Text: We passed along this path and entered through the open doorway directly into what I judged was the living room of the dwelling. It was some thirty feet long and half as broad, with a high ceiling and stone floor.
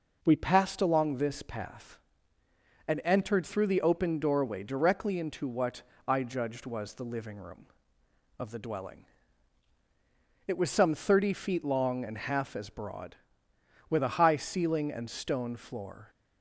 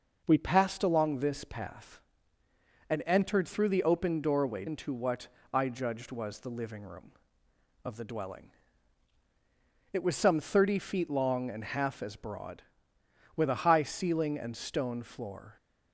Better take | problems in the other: first | skips "directly"; at 4.6 s // pauses between "what" and "I"; slight; at 5.2 s; 0.26 s long; slight in the first

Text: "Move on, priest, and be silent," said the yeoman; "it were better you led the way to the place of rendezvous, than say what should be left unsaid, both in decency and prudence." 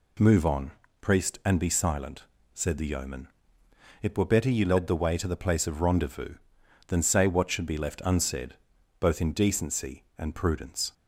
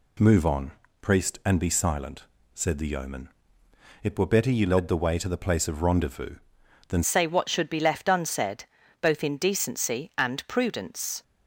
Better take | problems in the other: first | changes voice at "say"; from 7.0 s on; 4.2 s long

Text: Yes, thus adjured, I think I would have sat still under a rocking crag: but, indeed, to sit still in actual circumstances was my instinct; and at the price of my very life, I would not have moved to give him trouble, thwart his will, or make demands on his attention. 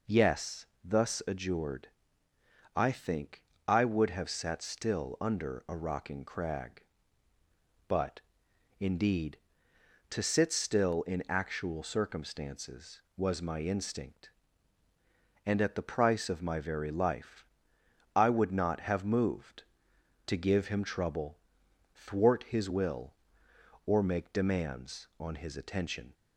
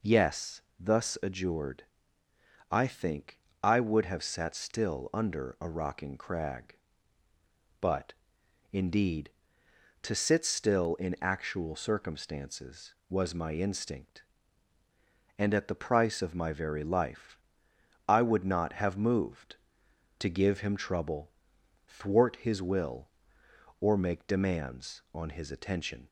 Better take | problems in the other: neither | pauses between "think" and "I"; slight; the same in both

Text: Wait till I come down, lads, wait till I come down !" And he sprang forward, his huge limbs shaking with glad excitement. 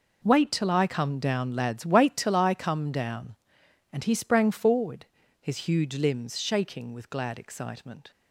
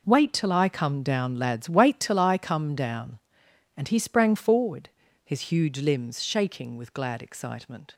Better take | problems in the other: neither | none

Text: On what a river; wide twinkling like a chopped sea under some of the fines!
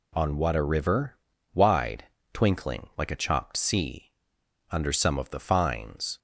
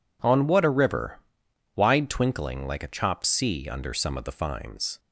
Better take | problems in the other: second | pauses between "wide" and "twinkling"; slight; at 2.0 s; 0.30 s long // pauses between "sea" and "under"; noticeable; at 4.1 s; 0.58 s long

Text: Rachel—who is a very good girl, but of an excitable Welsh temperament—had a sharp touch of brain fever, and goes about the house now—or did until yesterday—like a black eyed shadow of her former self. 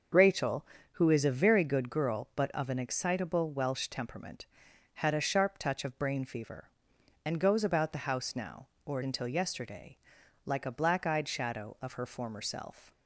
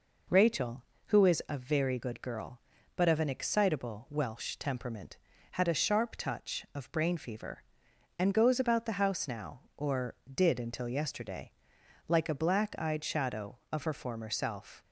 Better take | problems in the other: second | starts louder than the rest; noticeable; until 1.4 s; 6 dB // skips "did"; at 9.0 s

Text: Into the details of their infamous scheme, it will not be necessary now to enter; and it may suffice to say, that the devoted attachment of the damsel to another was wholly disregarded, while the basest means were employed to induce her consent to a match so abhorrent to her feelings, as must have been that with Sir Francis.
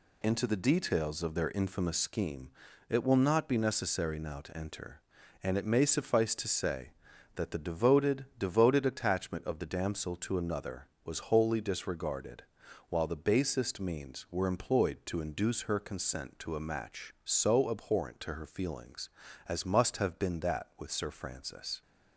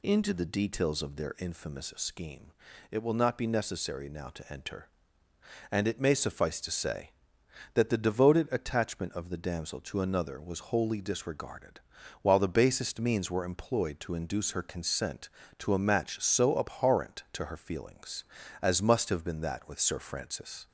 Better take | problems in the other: second | says "devoted" twice; at 8.3 s

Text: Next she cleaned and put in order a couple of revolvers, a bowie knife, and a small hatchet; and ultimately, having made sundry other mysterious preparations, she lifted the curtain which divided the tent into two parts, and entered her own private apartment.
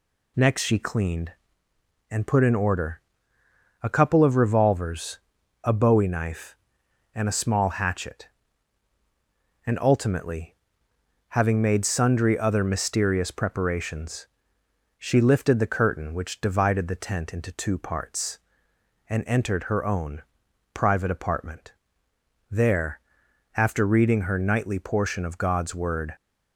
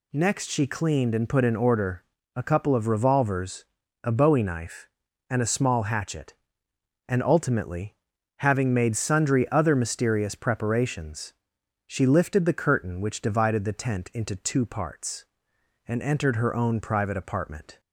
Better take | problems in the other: second | pauses between "order" and "a"; noticeable; at 3.0 s; 0.82 s long; slight in the second // pauses between "own" and "private"; noticeable; at 20.2 s; 0.50 s long // goes on to say "There after reading her nightly portion of God's Word"; strong; from 22.5 s on; 3.6 s long

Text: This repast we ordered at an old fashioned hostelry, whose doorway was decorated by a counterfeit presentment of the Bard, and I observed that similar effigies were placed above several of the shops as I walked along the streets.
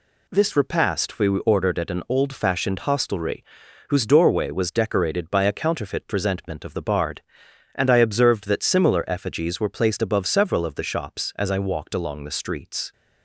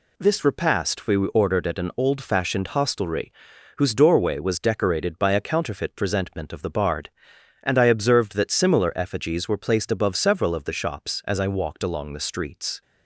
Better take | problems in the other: neither | none

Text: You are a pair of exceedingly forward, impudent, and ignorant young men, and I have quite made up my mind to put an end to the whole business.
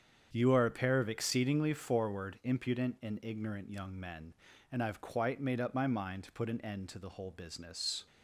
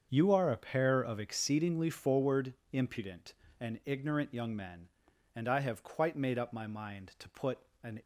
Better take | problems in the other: first | starts louder than the rest; until 1.1 s; 7 dB; strong in the first // pauses between "put" and "an"; slight; at 7.5 s; 0.24 s long // stops before "end to the whole business"; at 8.0 s

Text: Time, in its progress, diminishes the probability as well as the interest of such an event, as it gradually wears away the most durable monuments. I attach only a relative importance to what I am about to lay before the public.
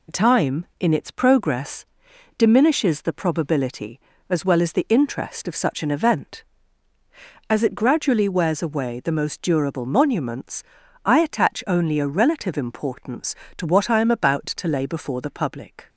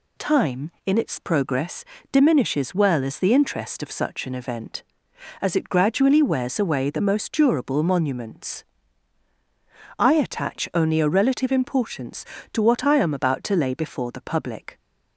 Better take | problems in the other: first | skips "the probability as"; at 2.7 s

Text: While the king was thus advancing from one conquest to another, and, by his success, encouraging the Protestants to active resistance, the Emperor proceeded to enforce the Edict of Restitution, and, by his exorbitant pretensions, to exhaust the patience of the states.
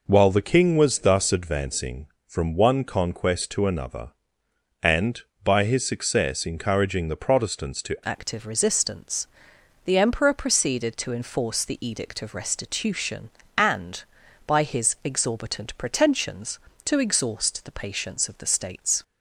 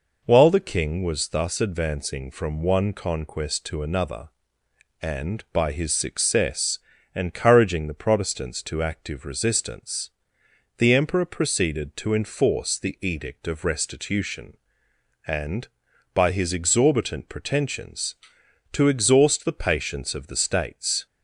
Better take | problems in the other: second | changes voice at "active"; from 8.0 s on; 11.0 s long

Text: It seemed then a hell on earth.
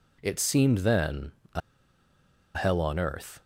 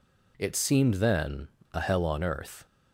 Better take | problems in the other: second | pauses between "then" and "a"; slight; at 1.3 s; 0.24 s long; slight in the second // pauses between "a" and "hell"; noticeable; at 1.6 s; 0.95 s long

